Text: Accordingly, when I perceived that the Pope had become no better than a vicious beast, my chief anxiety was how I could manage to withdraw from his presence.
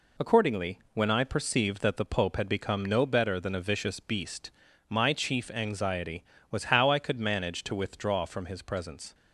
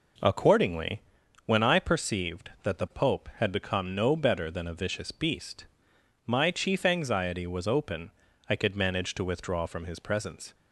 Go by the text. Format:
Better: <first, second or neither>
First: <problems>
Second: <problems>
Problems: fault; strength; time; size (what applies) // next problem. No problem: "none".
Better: first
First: none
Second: says "open" for "how"; at 7.6 s